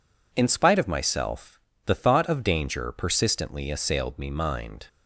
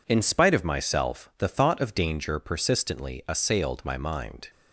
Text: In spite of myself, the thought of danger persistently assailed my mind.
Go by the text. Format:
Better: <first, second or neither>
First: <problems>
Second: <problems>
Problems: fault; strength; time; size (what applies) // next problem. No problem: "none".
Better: second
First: says "me" for "my"; at 4.1 s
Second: none